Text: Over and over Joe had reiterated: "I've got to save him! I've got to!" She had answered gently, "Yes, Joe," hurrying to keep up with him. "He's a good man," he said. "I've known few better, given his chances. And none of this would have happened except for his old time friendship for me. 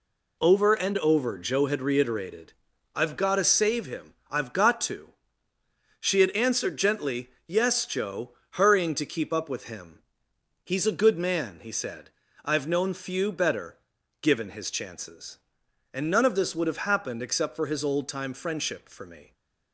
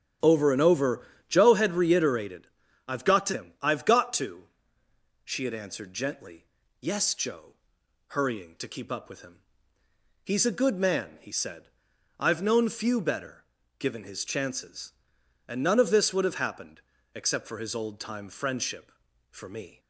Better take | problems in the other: first | starts louder than the rest; strong; until 1.5 s; 10 dB // pauses between "over" and "Joe"; slight; at 1.0 s; 0.26 s long // skips "save"; at 3.3 s // pauses between "happened" and "except"; slight; at 16.7 s; 0.36 s long

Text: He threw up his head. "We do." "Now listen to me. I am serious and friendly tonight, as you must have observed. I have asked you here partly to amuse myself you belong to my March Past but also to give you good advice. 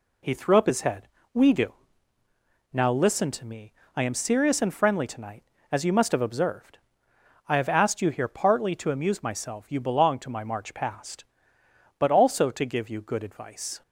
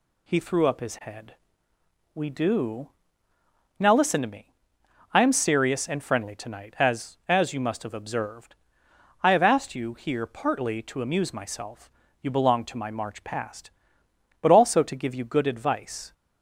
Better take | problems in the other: first | says "as" twice; at 7.2 s // pauses between "myself" and "you"; slight; at 11.8 s; 0.32 s long

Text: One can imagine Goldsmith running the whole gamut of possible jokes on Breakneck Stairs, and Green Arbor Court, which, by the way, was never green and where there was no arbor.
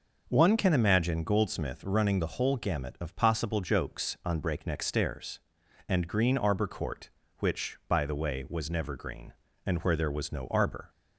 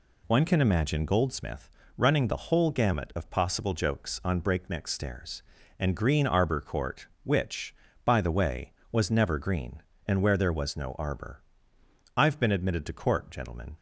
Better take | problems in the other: first | pauses between "Goldsmith" and "running"; slight; at 1.6 s; 0.30 s long // goes on to say "I've been admitted to Court gentlemen"; from 12.1 s on; 1.5 s long

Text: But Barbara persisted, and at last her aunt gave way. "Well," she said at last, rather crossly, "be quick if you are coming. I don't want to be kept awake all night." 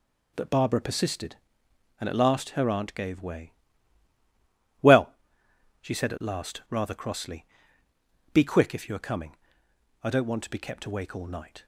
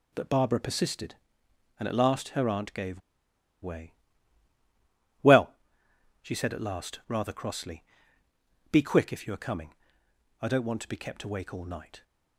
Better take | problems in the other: first | pauses between "gave" and "way"; noticeable; at 3.0 s; 0.62 s long

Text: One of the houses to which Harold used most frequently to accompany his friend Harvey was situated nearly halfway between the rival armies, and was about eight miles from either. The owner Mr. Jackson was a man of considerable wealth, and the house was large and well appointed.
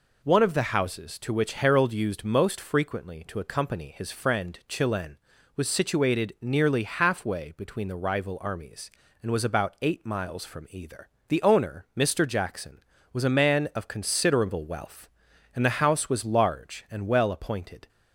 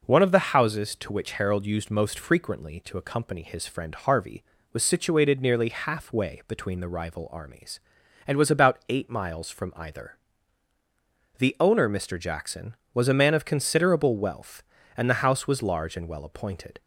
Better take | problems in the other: second | says "Chilen" for "Harvey"; at 4.6 s

